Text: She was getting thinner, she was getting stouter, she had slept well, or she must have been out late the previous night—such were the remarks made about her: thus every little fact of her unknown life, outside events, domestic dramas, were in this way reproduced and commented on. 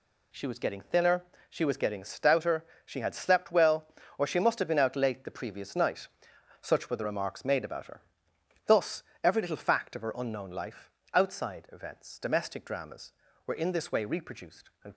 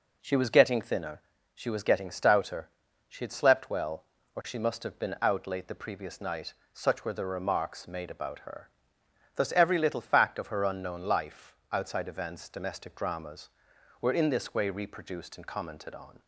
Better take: second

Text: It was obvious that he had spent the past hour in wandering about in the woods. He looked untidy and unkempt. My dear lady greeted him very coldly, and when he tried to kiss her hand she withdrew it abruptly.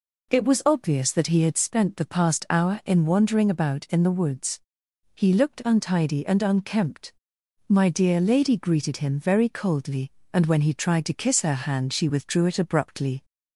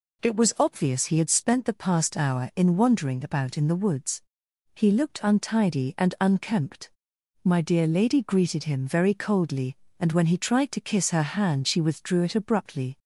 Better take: first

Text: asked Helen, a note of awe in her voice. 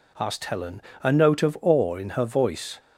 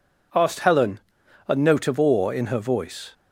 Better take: neither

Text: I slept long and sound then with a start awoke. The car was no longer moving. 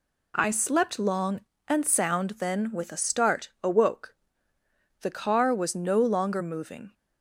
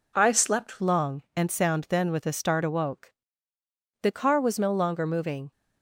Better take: first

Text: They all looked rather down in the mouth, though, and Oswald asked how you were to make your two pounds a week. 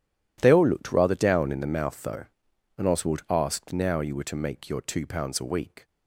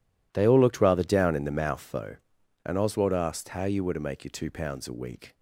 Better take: second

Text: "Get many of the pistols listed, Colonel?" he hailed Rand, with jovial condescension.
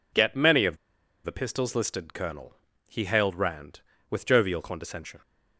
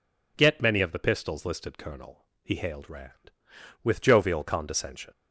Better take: second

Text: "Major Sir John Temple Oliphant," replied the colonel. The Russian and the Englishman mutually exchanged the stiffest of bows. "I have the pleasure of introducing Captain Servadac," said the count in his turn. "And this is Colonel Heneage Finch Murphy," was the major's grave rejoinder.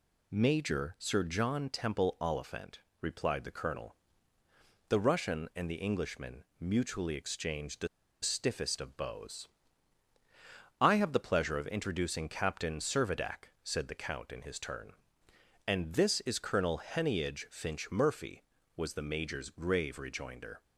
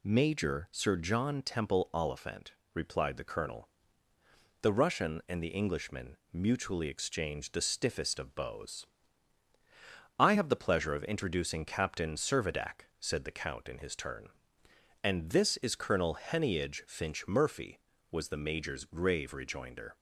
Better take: second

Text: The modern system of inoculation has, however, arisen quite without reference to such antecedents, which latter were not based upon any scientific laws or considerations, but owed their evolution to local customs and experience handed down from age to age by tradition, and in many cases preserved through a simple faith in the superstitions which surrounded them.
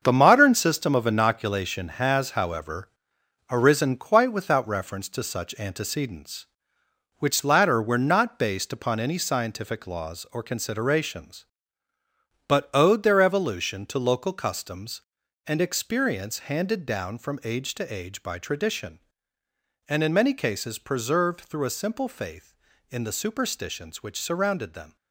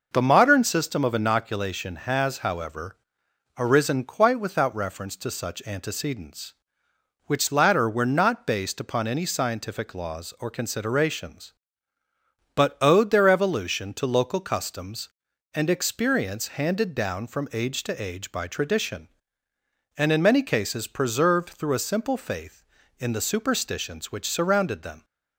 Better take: second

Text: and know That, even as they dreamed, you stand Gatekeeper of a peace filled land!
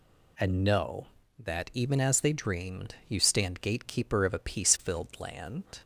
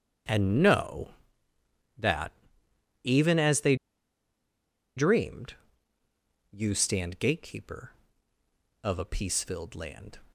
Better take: first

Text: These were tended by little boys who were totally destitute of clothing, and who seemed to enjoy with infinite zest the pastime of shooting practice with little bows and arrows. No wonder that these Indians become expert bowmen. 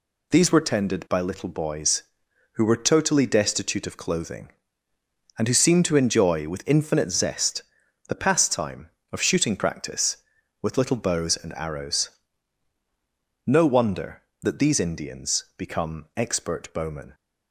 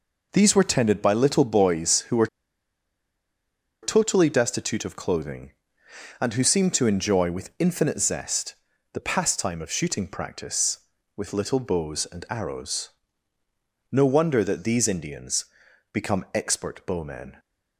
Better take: first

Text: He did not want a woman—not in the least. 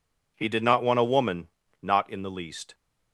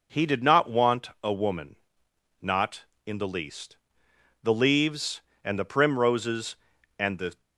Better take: first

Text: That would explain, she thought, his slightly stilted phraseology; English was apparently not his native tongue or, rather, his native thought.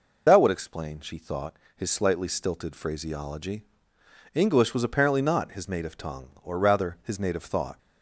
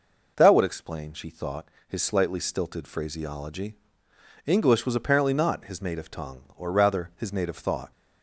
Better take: second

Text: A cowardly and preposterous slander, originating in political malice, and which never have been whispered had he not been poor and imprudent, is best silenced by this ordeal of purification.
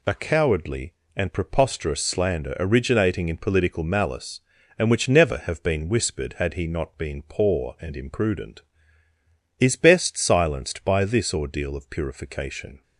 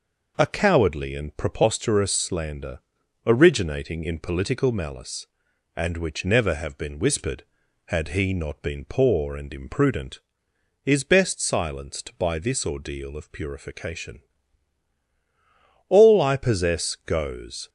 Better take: first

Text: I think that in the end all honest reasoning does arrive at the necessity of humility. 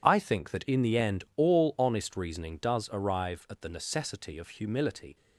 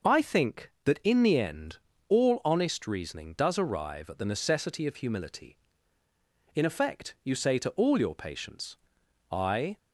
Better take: first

